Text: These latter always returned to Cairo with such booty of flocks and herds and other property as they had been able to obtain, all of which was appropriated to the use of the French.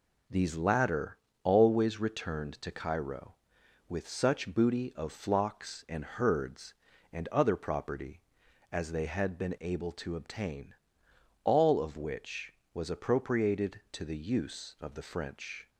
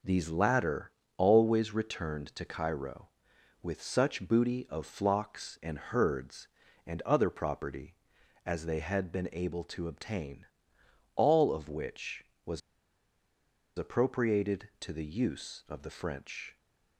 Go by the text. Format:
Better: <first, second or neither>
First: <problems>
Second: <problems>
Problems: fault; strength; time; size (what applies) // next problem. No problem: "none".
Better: first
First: pauses between "latter" and "always"; slight; at 1.1 s; 0.26 s long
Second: pauses between "latter" and "always"; slight; at 0.9 s; 0.26 s long // pauses between "was" and "appropriated"; at 12.6 s; 1.1 s long